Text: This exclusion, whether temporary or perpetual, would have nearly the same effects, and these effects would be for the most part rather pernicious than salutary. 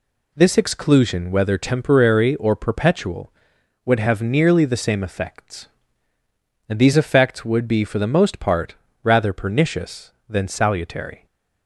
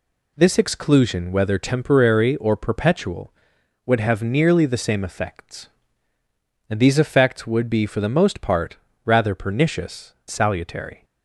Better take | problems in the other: first | pauses between "part" and "rather"; slight; at 8.7 s; 0.28 s long; slight in the first // skips "than"; at 10.2 s

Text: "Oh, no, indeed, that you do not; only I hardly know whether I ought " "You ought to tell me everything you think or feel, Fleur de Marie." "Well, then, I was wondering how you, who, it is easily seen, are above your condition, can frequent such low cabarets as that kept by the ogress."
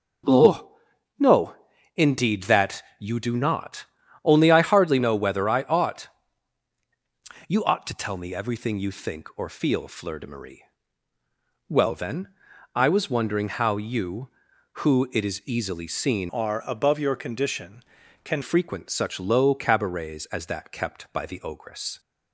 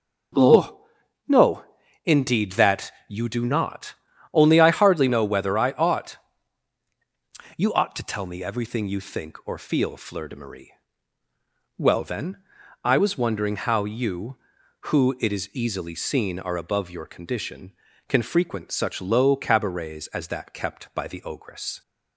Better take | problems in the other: second | starts louder than the rest; until 2.1 s; 6.5 dB; also in the second // pauses between "that" and "you"; slight; at 2.8 s; 0.16 s long; slight in the second // changes voice from "are" to "can"; from 16.2 to 18.4 s; 2.2 s long

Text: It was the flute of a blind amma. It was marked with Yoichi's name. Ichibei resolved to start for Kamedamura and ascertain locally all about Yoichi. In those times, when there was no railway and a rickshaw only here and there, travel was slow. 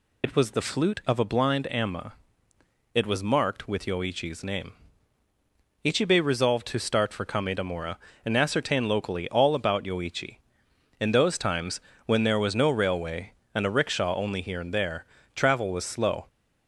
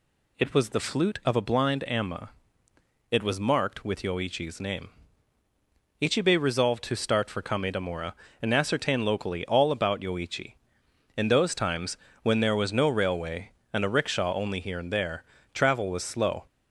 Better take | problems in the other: second | loses the start of "It"; at 0.2 s; 55 ms

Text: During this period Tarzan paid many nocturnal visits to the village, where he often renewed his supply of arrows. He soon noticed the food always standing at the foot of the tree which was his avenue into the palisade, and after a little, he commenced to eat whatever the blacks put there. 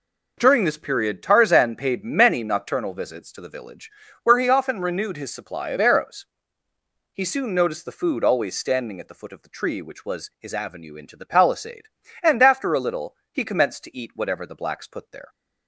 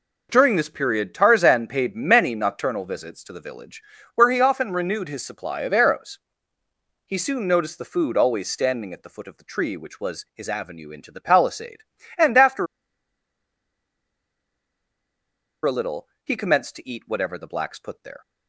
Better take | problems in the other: first | pauses between "after" and "a"; strong; at 12.6 s; 2.9 s long

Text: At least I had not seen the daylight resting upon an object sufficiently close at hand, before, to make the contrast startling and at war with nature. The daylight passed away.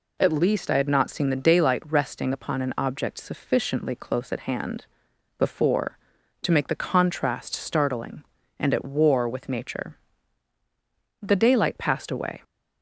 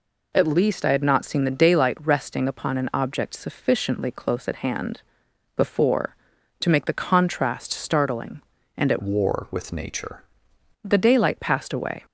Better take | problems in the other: first | changes voice from "war" to "nature"; from 9.0 to 10.2 s; 1.2 s long

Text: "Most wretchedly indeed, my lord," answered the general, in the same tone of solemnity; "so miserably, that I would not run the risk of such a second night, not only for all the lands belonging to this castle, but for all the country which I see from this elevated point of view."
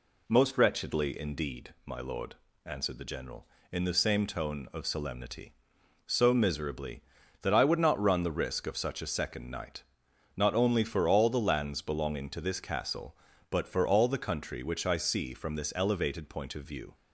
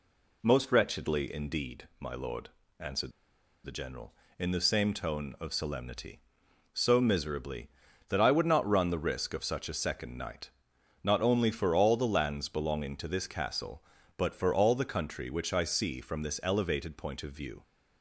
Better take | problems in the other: first | pauses between "answered" and "the"; noticeable; at 3.1 s; 0.53 s long

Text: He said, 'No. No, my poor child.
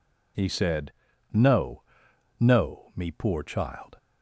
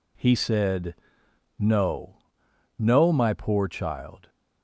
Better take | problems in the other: second | says "me" for "my"; at 2.9 s

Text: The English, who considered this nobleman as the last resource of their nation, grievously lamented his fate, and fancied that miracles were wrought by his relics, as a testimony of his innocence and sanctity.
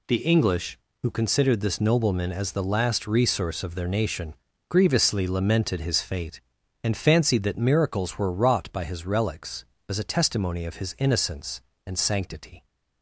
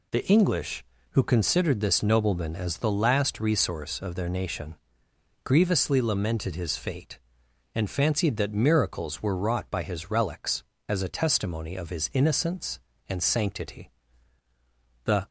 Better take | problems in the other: first | goes on to say "The"; slight; from 15.0 s on; 0.24 s long

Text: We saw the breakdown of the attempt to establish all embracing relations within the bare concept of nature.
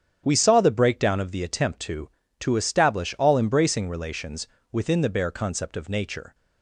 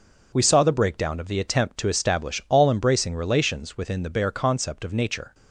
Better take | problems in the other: second | starts louder than the rest; strong; until 1.2 s; 9 dB // says "to" twice; at 2.4 s // pauses between "relations" and "within"; slight; at 4.4 s; 0.26 s long

